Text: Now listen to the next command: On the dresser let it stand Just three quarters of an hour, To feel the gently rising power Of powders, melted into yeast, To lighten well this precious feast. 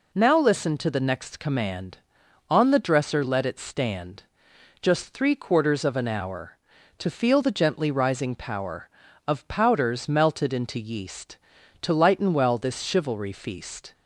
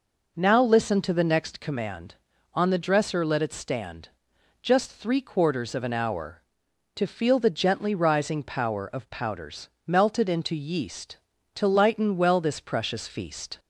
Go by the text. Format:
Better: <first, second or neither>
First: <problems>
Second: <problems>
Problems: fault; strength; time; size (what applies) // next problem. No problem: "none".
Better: second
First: pauses between "stand" and "Just"; noticeable; at 4.2 s; 0.58 s long // says "chivalry" for "precious"; at 12.8 s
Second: pauses between "stand" and "Just"; noticeable; at 4.0 s; 0.54 s long